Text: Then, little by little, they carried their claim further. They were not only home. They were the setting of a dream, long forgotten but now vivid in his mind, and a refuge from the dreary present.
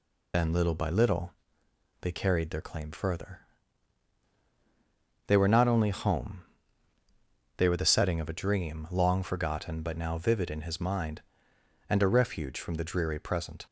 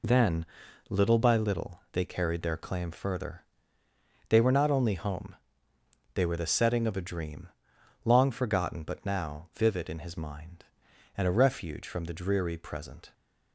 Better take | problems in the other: second | loses the start of "Then"; at 0.3 s; 65 ms

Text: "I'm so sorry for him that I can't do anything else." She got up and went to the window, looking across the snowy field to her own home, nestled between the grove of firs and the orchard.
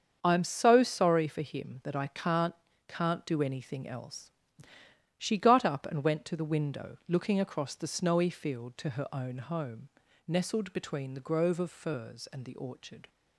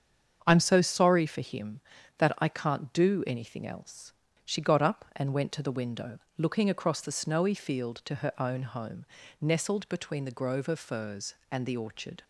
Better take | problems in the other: second | starts louder than the rest; until 1.2 s; 7 dB; strong in the second // says "can't" twice; at 2.8 s

